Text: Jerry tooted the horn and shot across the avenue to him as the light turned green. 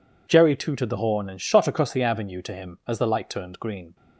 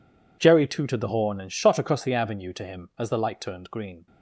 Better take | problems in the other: first | gets quieter; strong; throughout; 20 dB

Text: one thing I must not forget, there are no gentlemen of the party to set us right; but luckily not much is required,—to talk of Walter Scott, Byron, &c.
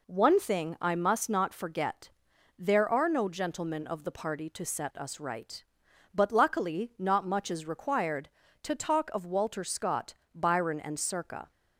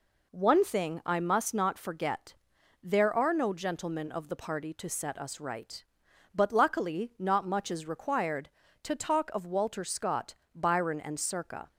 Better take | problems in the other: neither | none

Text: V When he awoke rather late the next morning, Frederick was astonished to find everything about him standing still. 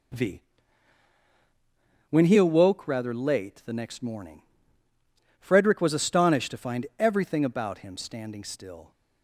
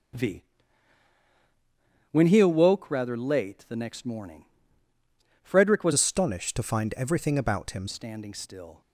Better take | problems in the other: first | starts louder than the rest; until 2.8 s; 7 dB // pauses between "V" and "When"; strong; at 0.4 s; 1.7 s long; strong in the first // changes voice from "astonished" to "him"; from 5.9 to 7.8 s; 1.9 s long

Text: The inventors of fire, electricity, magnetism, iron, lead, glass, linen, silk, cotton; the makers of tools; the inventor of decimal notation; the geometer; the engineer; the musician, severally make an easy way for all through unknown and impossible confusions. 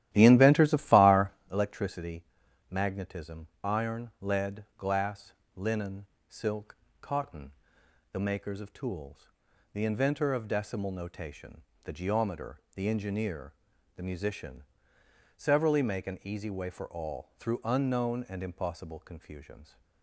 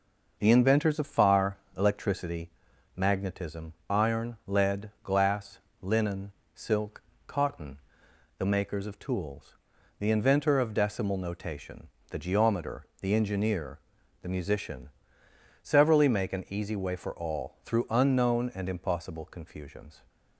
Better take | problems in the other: second | starts louder than the rest; strong; until 1.4 s; 13 dB

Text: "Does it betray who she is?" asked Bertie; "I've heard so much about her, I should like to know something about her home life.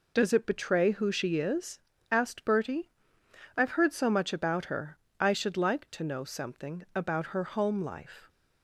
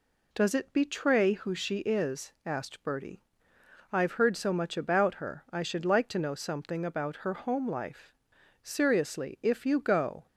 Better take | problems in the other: first | goes on to say "Seriously if you go"; from 8.6 s on; 1.6 s long

